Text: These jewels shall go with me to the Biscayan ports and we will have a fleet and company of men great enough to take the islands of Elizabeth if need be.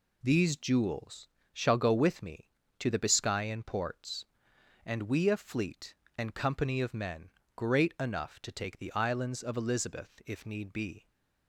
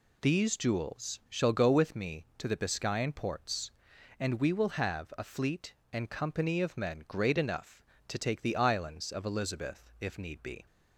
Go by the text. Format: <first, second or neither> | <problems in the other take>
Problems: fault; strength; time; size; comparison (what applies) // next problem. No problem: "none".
second | pauses between "jewels" and "shall"; slight; at 1.2 s; 0.24 s long // skips "will have"; at 5.2 s // pauses between "men" and "great"; slight; at 7.3 s; 0.24 s long